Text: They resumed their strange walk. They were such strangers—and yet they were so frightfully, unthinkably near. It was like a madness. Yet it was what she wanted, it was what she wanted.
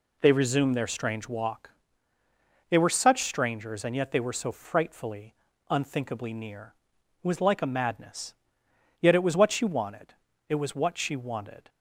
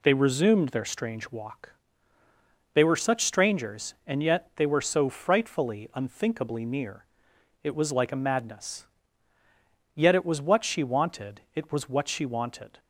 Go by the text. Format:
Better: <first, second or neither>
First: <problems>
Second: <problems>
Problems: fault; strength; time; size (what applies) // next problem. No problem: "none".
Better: neither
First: none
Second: none